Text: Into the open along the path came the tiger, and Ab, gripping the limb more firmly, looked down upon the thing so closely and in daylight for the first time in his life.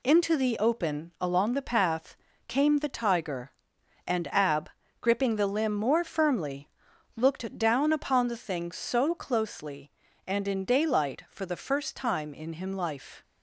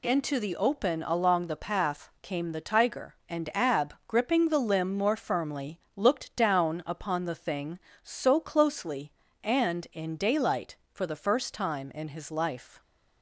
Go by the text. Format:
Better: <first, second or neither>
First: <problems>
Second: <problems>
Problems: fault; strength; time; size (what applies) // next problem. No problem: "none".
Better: second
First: pauses between "path" and "came"; slight; at 2.1 s; 0.32 s long // says "him" for "his"; at 12.5 s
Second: none